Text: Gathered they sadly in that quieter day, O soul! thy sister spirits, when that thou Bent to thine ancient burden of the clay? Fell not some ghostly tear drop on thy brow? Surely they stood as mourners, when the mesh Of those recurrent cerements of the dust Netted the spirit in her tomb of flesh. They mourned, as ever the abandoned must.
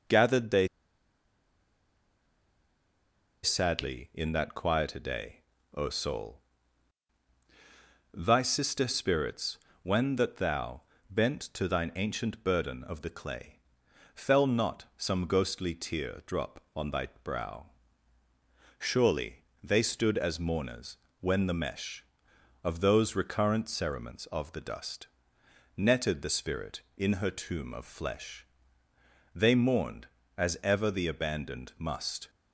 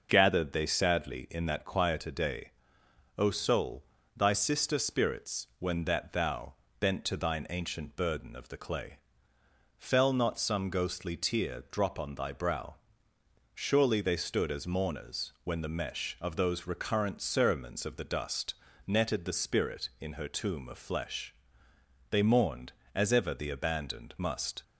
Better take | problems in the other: second | pauses between "they" and "sadly"; strong; at 0.6 s; 2.7 s long // pauses between "thou" and "Bent"; slight; at 10.8 s; 0.30 s long; slight in the second // pauses between "thy" and "brow"; slight; at 17.0 s; 0.16 s long // pauses between "Surely" and "they"; slight; at 19.4 s; 0.20 s long // pauses between "dust" and "Netted"; noticeable; at 25.0 s; 0.68 s long; slight in the second

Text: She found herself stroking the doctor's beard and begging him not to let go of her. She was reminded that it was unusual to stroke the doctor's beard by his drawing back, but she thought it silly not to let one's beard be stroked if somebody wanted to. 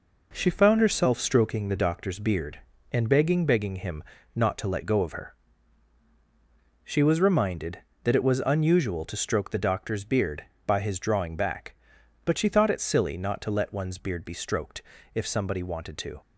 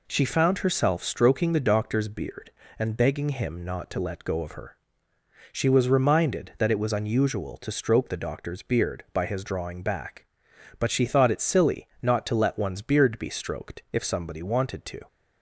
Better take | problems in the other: second | says "begging" twice; at 3.4 s // pauses between "him" and "not"; slight; at 4.0 s; 0.32 s long // pauses between "stroked" and "if"; slight; at 14.8 s; 0.32 s long

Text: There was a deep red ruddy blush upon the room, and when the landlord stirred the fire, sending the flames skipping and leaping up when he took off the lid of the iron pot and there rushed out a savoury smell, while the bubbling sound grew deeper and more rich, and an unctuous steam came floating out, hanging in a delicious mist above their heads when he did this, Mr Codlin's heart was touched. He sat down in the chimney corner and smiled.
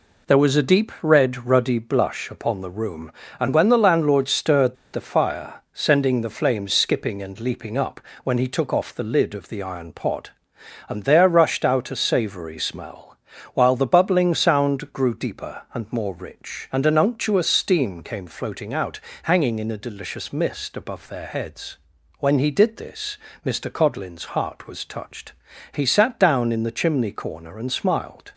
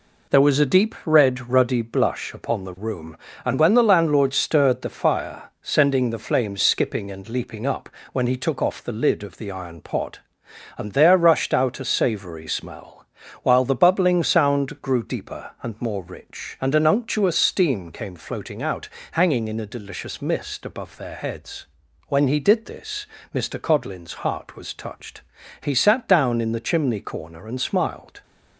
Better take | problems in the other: second | pauses between "stirred" and "the"; slight; at 4.7 s; 0.17 s long // pauses between "up" and "when"; slight; at 8.0 s; 0.22 s long; slight in the second // pauses between "heads" and "when"; at 21.7 s; 0.42 s long; also in the second

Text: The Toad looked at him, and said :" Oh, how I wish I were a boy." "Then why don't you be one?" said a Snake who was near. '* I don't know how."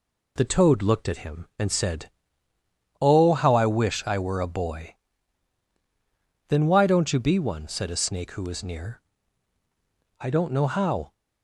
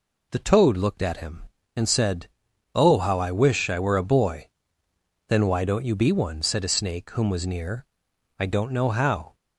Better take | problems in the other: first | says "whom" for "who"; at 7.1 s

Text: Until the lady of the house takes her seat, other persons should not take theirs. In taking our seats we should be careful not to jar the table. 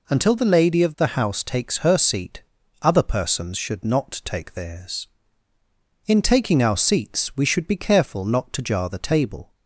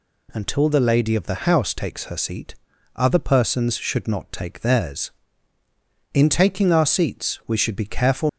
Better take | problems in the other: first | stops before "not to jar the table"; at 8.2 s

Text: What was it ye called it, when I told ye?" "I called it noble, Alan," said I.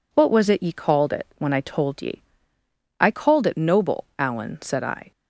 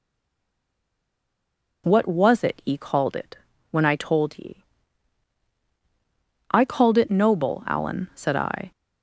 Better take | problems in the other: first | stays silent before the first word; noticeable; until 1.8 s; 1.8 s long

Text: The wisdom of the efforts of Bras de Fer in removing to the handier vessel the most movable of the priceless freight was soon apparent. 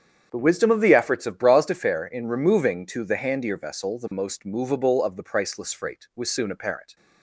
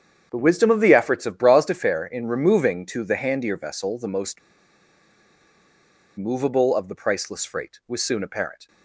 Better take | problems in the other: first | starts louder than the rest; strong; until 1.3 s; 8 dB; strong in the first // pauses between "most" and "movable"; strong; at 4.4 s; 1.7 s long

